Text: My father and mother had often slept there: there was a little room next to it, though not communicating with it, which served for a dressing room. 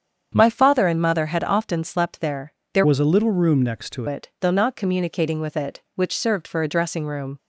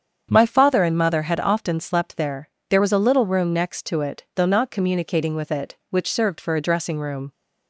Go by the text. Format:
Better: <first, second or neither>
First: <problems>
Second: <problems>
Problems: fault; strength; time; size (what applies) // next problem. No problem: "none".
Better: second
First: starts louder than the rest; strong; until 1.3 s; 8 dB // changes voice from "was" to "to"; from 2.8 to 4.0 s; 1.2 s long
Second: starts louder than the rest; strong; until 1.3 s; 7.5 dB